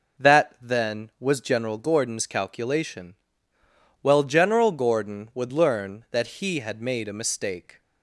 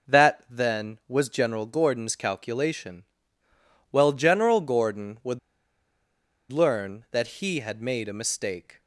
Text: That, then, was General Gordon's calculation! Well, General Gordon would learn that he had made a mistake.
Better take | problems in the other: first | pauses between "would" and "learn"; at 5.3 s; 1.1 s long

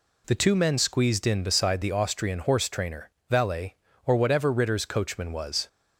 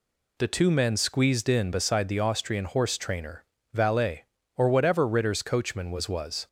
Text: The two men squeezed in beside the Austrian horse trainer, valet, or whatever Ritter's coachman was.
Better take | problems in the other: first | says "was" twice; at 6.0 s

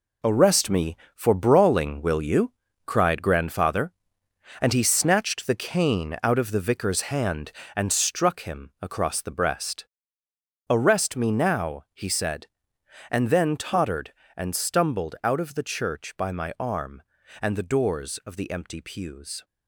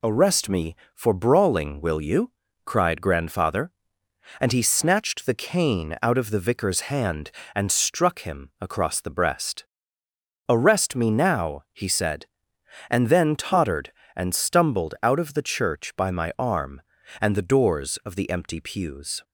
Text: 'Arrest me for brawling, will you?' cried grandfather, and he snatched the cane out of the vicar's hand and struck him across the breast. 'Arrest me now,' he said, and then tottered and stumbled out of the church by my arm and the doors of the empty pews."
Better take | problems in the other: second | gets quieter; strong; throughout; 8.5 dB

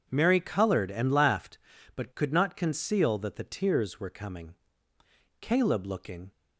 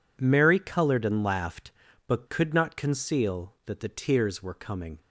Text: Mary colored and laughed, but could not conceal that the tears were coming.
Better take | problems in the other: second | goes on to say "Caleb looking"; noticeable; from 5.3 s on; 0.92 s long

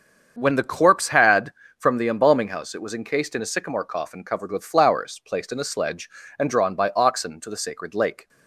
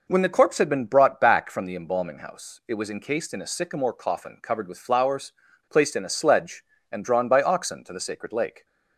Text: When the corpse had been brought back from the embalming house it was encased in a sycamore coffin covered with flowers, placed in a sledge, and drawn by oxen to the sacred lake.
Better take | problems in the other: second | starts louder than the rest; until 1.3 s; 7 dB // skips "been brought back"; at 1.6 s

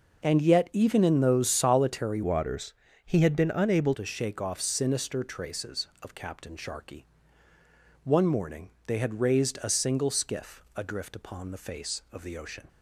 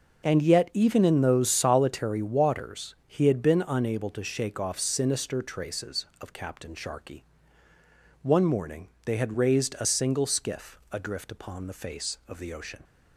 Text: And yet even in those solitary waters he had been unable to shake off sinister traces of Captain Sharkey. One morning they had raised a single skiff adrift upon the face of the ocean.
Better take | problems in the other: second | changes voice from "waters" to "unable"; from 2.2 to 3.9 s; 1.7 s long // pauses between "waters" and "he"; slight; at 2.7 s; 0.32 s long // pauses between "morning" and "they"; slight; at 8.6 s; 0.16 s long; slight in the second

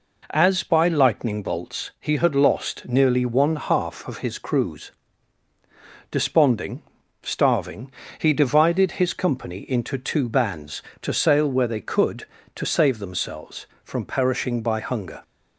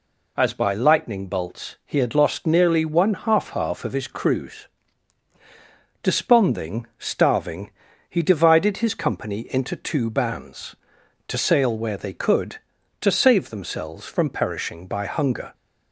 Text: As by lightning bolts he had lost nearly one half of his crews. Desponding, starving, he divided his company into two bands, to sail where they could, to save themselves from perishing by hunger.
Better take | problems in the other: first | says "half" twice; at 3.5 s

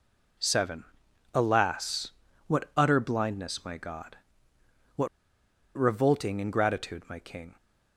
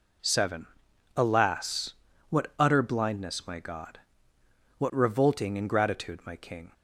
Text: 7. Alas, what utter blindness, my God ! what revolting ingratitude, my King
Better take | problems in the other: second | pauses between "what" and "revolting"; noticeable; at 5.0 s; 0.70 s long

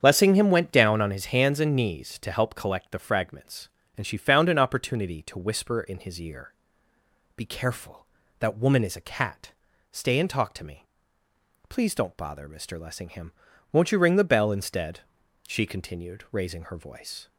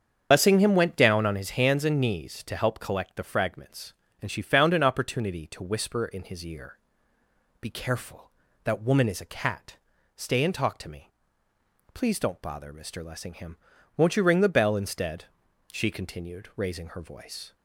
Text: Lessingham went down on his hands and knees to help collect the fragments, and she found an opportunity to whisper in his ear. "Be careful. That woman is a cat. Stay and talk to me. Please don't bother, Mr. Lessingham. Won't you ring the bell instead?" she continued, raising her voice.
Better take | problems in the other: first | loses the start of "Lessingham"; at 0.3 s; 35 ms // starts louder than the rest; strong; until 1.3 s; 7.5 dB; strong in the first

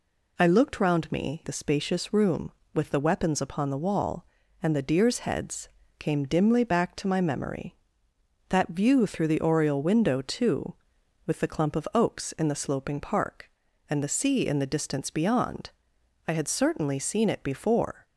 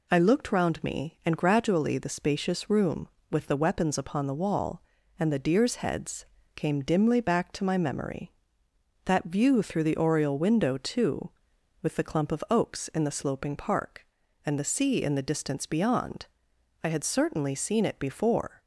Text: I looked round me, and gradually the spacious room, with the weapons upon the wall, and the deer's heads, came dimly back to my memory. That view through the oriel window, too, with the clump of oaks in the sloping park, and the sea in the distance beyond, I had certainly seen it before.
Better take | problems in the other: second | skips "and gradually"; at 1.4 s

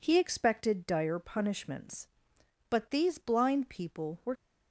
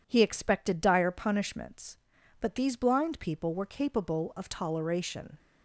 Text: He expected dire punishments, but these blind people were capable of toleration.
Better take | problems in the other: second | stops before "capable of toleration"; at 4.3 s

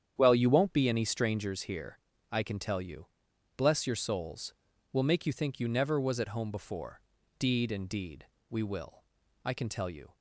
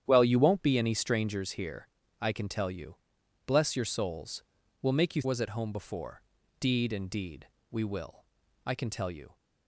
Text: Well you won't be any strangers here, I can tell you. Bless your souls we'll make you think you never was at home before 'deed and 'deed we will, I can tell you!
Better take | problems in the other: first | starts louder than the rest; strong; until 1.0 s; 9.5 dB; strong in the first // pauses between "souls" and "we'll"; at 4.4 s; 0.40 s long; also in the first // skips "think you never"; at 5.2 s // pauses between "before" and "deed"; at 6.2 s; 0.38 s long; also in the first // pauses between "deed" and "we"; slight; at 7.4 s; 0.24 s long; slight in the first

